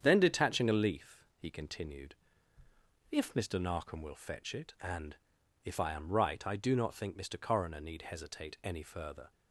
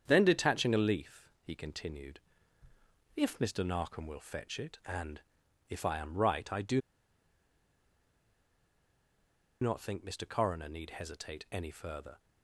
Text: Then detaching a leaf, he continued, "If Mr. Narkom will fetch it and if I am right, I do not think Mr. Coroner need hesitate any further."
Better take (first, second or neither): first